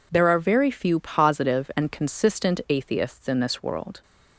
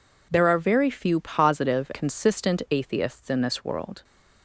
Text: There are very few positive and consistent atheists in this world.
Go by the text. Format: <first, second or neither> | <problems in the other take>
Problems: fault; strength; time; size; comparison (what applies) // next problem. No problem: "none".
first | skips "and"; at 1.9 s